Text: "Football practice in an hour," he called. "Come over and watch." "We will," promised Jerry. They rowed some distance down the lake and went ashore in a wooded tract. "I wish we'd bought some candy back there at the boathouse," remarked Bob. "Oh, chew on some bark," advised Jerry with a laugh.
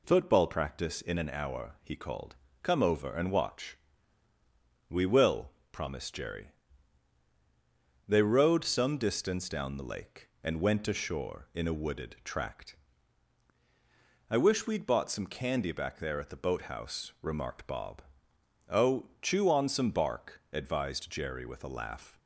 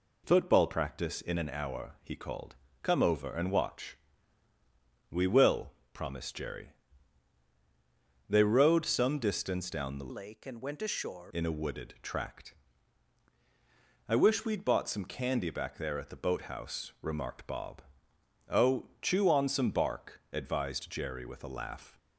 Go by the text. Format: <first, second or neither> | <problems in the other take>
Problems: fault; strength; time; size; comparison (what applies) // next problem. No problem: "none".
first | changes voice from "lake" to "ashore"; from 10.1 to 11.3 s; 1.2 s long